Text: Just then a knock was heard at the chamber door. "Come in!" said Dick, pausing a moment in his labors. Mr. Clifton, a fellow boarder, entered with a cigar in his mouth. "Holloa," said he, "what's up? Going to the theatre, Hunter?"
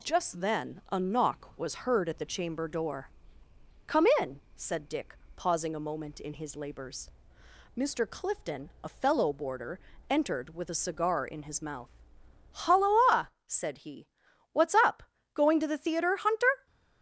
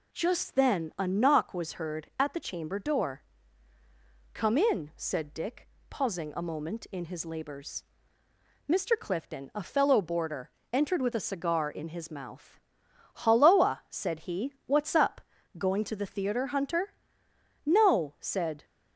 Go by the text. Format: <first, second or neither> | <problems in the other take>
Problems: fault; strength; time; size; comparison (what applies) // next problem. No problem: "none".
first | goes on to say "No said"; noticeable; from 17.6 s on; 0.98 s long